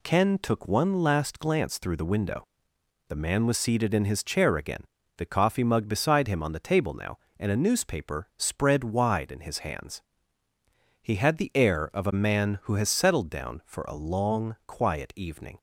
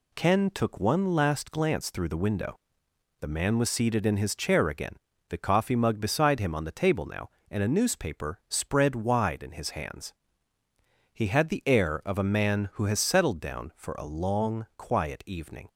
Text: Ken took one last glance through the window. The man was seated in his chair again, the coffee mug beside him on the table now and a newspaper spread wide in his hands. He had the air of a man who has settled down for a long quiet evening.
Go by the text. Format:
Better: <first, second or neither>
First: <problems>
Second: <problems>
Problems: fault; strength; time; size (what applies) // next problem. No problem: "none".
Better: neither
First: none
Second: none